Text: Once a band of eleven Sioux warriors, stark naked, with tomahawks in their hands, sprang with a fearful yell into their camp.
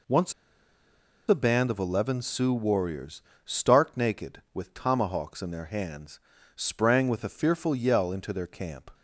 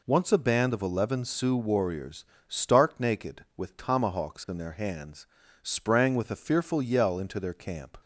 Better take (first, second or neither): second